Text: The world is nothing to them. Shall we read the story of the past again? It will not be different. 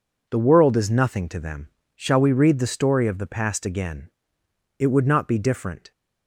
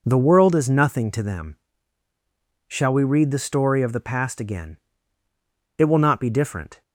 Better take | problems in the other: second | says "would" for "will"; at 4.8 s

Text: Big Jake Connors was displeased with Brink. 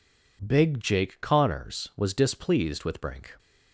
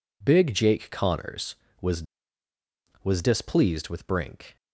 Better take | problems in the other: first | says "was" twice; at 3.0 s

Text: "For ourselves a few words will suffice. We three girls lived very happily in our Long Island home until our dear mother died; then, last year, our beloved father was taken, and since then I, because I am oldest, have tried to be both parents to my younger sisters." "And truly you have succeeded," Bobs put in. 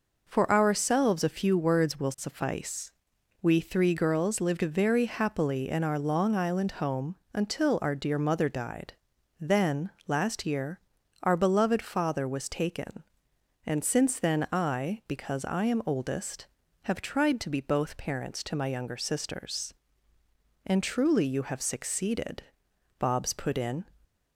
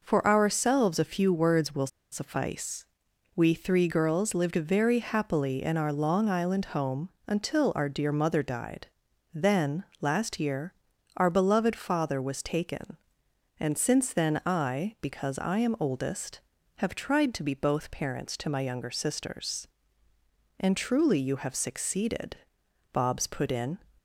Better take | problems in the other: first | pauses between "will" and "suffice"; slight; at 1.8 s; 0.24 s long // pauses between "home" and "until"; slight; at 7.0 s; 0.18 s long; slight in the first

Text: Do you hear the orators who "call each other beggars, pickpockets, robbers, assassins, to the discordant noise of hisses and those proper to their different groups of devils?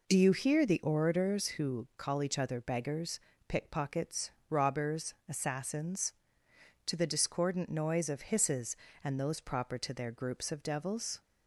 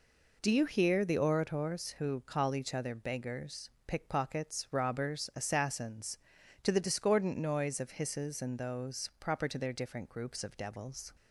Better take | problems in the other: second | skips "different"; at 10.1 s

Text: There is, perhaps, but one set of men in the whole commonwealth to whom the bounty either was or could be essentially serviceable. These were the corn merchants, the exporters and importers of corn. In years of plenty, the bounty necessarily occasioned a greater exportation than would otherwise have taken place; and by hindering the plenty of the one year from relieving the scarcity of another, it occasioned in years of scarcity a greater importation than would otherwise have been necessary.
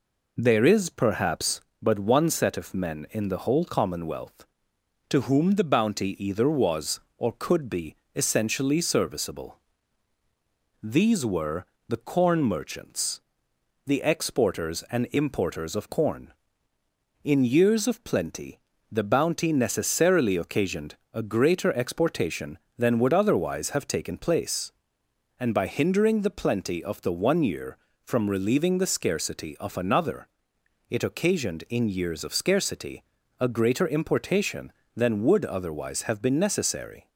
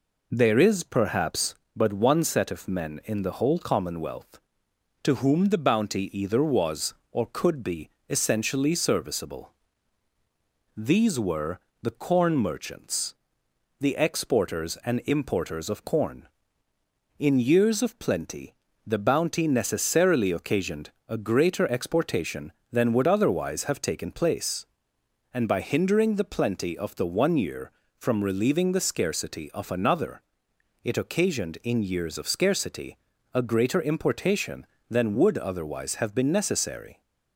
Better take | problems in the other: neither | pauses between "be" and "essentially"; slight; the same in both // pauses between "were" and "the"; slight; the same in both // pauses between "occasioned" and "a"; slight; the same in both // pauses between "scarcity" and "a"; the same in both

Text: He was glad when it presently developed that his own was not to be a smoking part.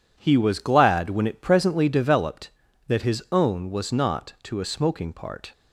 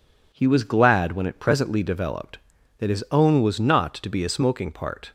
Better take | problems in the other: second | skips "be"; at 4.6 s

